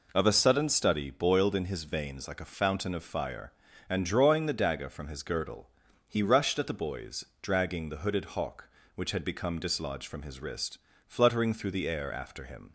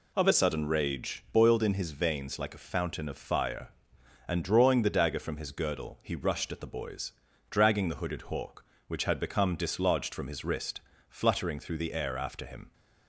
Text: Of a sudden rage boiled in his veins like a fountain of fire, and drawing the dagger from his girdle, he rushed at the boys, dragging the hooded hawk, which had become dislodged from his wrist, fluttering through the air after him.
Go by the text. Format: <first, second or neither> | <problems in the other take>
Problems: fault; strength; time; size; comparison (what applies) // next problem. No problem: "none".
second | says "study" for "rage"; at 0.6 s